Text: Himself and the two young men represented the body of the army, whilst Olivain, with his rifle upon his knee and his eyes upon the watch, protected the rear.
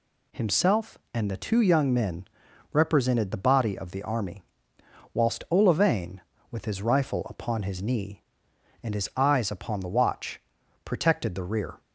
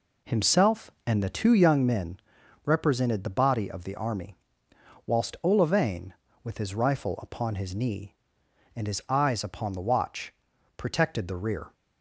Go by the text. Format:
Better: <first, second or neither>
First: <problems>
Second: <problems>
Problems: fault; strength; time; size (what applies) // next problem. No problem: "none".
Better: first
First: pauses between "men" and "represented"; noticeable; at 2.2 s; 0.46 s long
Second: starts louder than the rest; slight; until 2.0 s; 3.5 dB // pauses between "men" and "represented"; noticeable; at 2.1 s; 0.46 s long